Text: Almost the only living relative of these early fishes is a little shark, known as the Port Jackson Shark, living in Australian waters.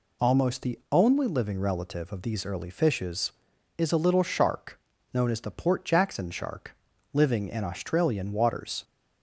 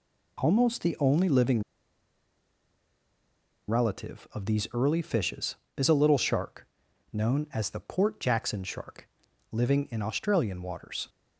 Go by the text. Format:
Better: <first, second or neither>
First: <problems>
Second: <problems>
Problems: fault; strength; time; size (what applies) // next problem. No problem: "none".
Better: first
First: none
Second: pauses between "living" and "relative"; strong; at 1.6 s; 2.0 s long